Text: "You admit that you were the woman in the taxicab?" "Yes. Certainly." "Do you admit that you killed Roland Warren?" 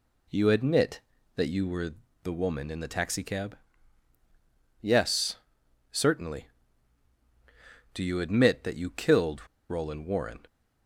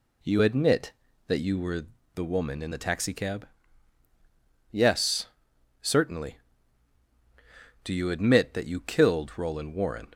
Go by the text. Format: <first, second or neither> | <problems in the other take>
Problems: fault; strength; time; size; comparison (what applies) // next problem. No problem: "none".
second | pauses between "were" and "the"; slight; at 1.9 s; 0.30 s long; slight in the second // pauses between "killed" and "Roland"; slight; at 9.4 s; 0.22 s long